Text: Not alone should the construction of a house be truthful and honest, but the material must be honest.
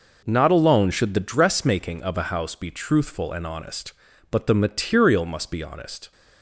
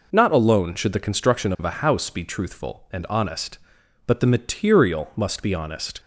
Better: second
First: says "dressmaking" for "construction"; at 1.2 s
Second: none

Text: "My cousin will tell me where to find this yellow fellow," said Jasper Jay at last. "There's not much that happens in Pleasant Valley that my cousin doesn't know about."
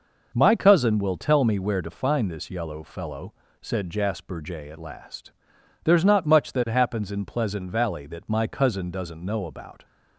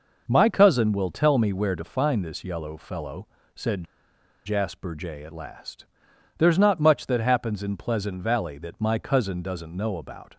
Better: first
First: none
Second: pauses between "said" and "Jasper"; noticeable; at 3.8 s; 0.62 s long

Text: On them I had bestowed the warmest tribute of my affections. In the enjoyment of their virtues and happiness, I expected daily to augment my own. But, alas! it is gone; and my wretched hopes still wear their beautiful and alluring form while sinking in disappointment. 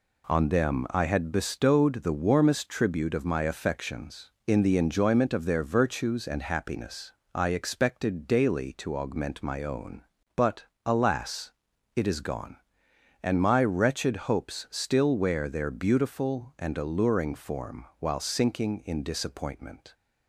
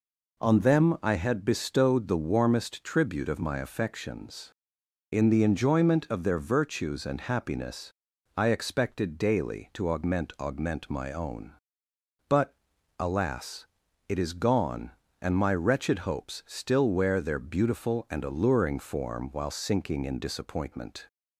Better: first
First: none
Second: says "augment" twice; at 10.3 s

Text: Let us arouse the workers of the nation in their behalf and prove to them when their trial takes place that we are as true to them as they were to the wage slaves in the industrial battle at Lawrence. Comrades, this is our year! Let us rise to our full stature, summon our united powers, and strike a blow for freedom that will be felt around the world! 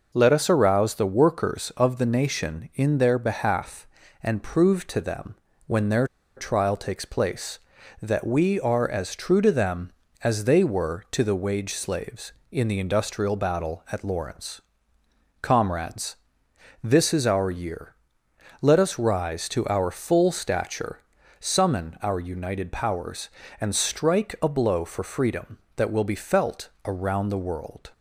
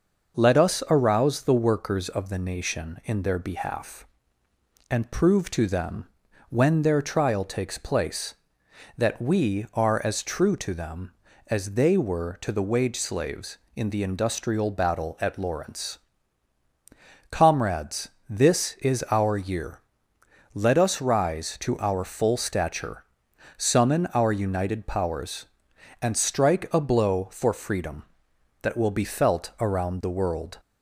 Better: second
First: pauses between "them" and "when"; slight; at 5.3 s; 0.32 s long // pauses between "their" and "trial"; slight; at 6.0 s; 0.31 s long // pauses between "felt" and "around"; slight; at 26.6 s; 0.16 s long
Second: pauses between "them" and "when"; at 6.0 s; 0.40 s long

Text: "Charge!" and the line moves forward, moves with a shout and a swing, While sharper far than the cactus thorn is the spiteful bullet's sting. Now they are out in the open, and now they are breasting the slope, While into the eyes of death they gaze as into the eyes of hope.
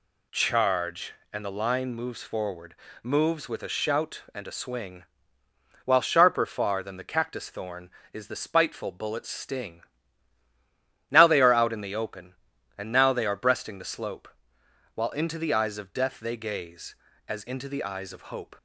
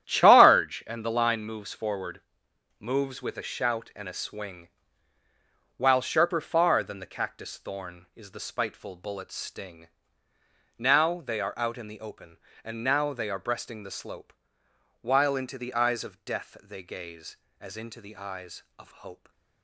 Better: first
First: none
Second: gets quieter; strong; throughout; 11 dB

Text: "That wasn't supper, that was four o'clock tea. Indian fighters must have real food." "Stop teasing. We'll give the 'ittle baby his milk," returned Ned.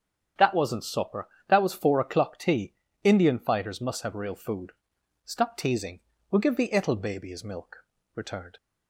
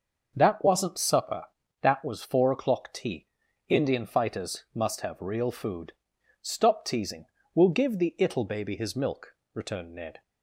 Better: second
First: starts louder than the rest; strong; until 1.5 s; 8 dB // stops before "Ned"; at 8.5 s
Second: starts louder than the rest; noticeable; until 1.3 s; 6 dB

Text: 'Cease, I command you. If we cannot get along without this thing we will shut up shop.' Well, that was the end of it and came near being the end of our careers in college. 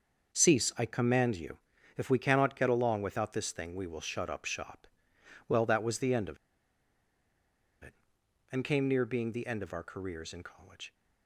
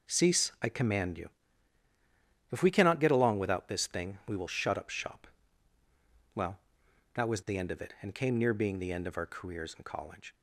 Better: second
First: starts louder than the rest; until 1.4 s; 6 dB // pauses between "of" and "it"; strong; at 6.3 s; 1.4 s long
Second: none

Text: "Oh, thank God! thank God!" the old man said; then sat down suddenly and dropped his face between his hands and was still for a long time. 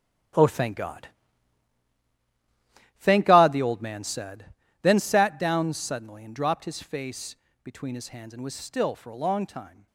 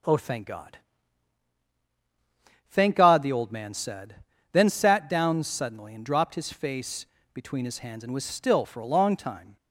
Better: second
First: gets quieter; strong; throughout; 12.5 dB // pauses between "face" and "between"; slight; at 7.3 s; 0.26 s long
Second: pauses between "face" and "between"; slight; at 7.0 s; 0.26 s long

